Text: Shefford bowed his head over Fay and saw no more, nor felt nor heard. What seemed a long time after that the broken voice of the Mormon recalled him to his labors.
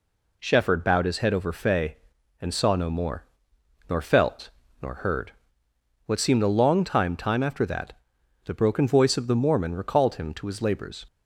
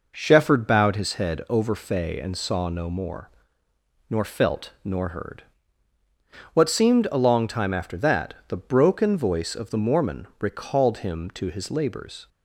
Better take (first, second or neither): second